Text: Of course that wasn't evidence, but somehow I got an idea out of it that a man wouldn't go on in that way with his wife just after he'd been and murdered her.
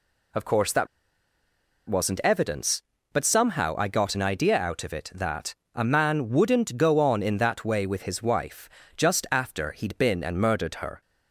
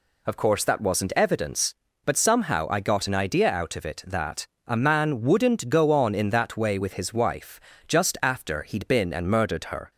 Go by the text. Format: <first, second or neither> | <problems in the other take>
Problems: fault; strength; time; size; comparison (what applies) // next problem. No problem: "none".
second | pauses between "that" and "wasn't"; at 0.8 s; 1.0 s long // pauses between "that" and "a"; slight; at 5.5 s; 0.22 s long; slight in the second // pauses between "wife" and "just"; slight; at 8.6 s; 0.28 s long; slight in the second